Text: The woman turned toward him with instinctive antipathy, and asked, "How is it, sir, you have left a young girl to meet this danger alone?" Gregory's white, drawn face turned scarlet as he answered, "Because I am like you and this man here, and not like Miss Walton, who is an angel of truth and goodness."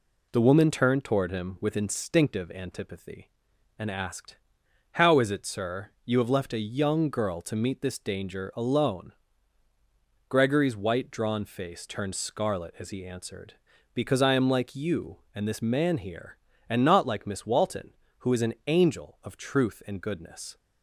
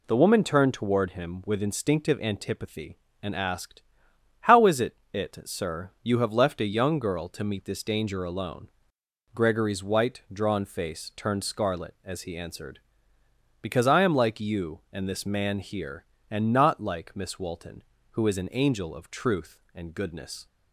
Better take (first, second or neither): first